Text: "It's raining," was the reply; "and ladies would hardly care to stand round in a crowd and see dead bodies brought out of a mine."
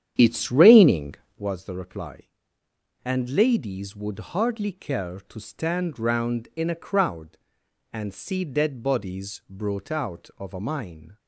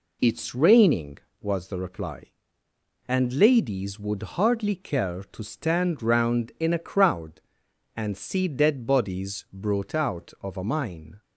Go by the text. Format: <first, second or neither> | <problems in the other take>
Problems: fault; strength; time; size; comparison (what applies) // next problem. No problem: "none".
second | starts louder than the rest; strong; until 1.5 s; 9.5 dB